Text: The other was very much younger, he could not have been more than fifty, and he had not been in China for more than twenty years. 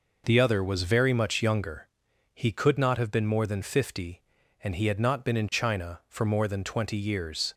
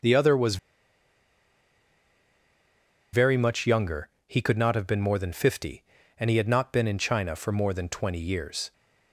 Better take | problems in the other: first | pauses between "was" and "very"; strong; at 0.5 s; 2.5 s long

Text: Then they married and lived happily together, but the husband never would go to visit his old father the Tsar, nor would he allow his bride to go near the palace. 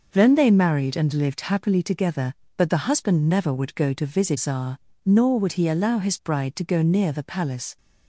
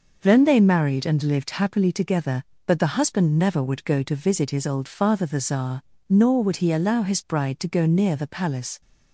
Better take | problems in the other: second | skips "his old father the"; at 4.3 s

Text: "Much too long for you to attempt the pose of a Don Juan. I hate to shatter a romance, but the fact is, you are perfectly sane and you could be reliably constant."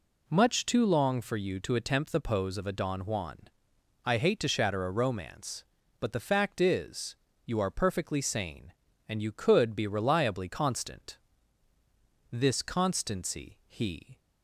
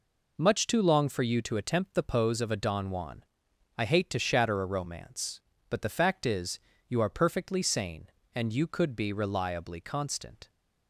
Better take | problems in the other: second | goes on to say "This constancy he"; strong; from 12.3 s on; 1.8 s long

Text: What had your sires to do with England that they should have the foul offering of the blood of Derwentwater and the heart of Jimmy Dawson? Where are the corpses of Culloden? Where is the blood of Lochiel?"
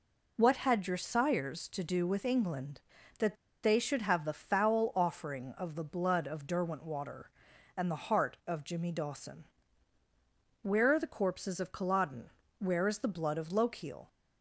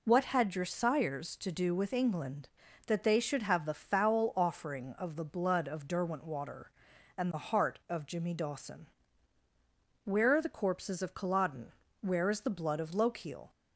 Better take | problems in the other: second | pauses between "that" and "they"; slight; at 3.3 s; 0.27 s long

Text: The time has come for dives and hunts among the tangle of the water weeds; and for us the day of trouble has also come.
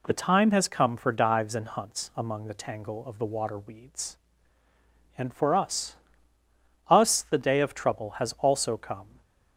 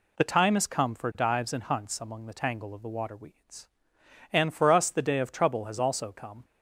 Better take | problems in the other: second | says "us" twice; at 6.8 s

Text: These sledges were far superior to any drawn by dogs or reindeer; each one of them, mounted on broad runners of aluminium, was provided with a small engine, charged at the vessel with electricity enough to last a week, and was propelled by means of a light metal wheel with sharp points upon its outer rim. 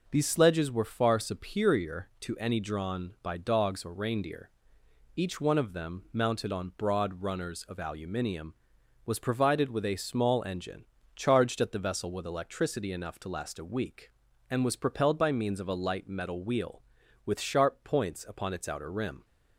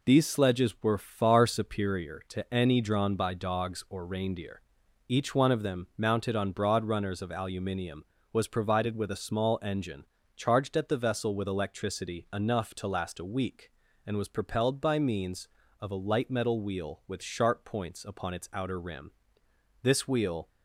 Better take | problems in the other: first | goes on to say "This wheel"; noticeable; from 19.8 s on; 0.64 s long

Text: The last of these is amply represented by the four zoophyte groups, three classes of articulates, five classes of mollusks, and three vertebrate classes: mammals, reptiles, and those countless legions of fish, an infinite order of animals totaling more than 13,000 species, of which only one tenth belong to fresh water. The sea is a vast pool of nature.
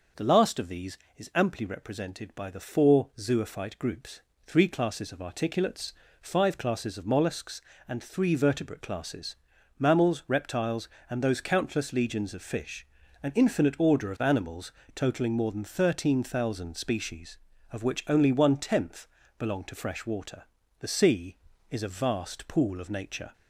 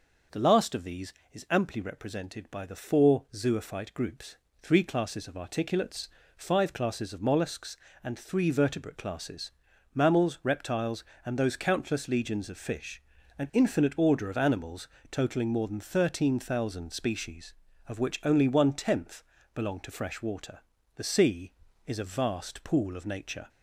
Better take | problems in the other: neither | pauses between "animals" and "totaling"; slight; the same in both // pauses between "tenth" and "belong"; slight; the same in both

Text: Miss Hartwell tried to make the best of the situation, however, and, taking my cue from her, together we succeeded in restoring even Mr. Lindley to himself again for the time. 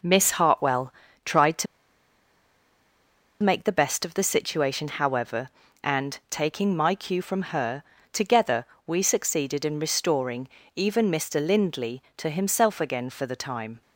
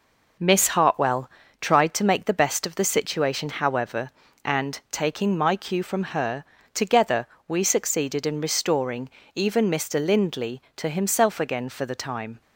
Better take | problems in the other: second | pauses between "Hartwell" and "tried"; slight; at 0.9 s; 0.34 s long; slight in the second // pauses between "to" and "make"; strong; at 1.6 s; 1.7 s long // pauses between "together" and "we"; slight; at 8.6 s; 0.22 s long; slight in the second // pauses between "restoring" and "even"; slight; at 10.4 s; 0.30 s long; slight in the second

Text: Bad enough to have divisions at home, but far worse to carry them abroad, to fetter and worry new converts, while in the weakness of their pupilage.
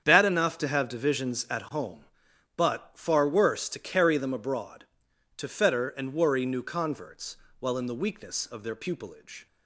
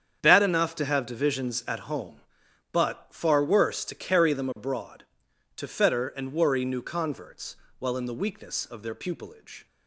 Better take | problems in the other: neither | starts louder than the rest; strong; the same in both

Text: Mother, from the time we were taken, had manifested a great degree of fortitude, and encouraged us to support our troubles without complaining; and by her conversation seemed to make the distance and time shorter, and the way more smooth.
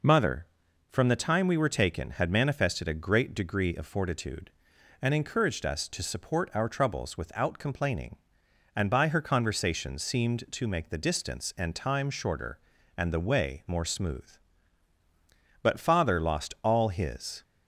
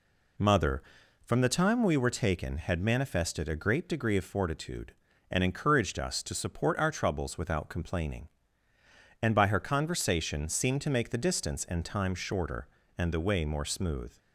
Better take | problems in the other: second | goes on to say "But father lost all his"; strong; from 15.6 s on; 1.8 s long

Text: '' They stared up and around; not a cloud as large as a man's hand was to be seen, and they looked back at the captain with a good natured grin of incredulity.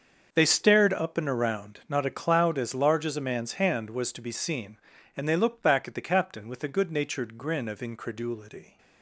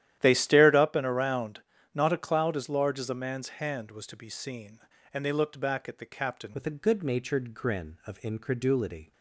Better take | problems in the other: first | starts louder than the rest; strong; until 1.1 s; 11.5 dB; also in the first // changes voice at "with"; from 6.5 s on; 2.6 s long

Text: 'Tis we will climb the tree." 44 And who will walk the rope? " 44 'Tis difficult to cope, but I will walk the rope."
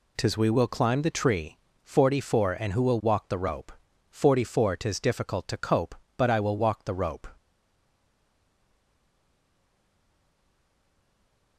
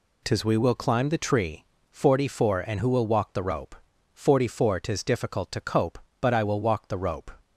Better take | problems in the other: second | stays silent after the last word; strong; from 7.3 s on; 4.2 s long

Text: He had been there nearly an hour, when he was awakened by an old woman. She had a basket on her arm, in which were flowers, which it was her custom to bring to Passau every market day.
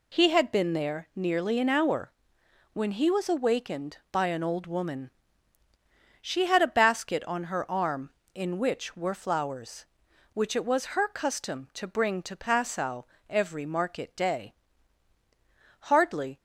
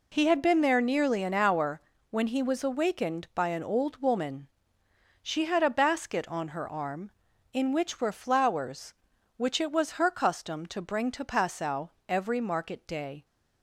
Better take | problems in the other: second | pauses between "Passau" and "every"; slight; at 13.0 s; 0.18 s long; slight in the second // goes on to say "Hardly"; from 15.7 s on; 0.58 s long

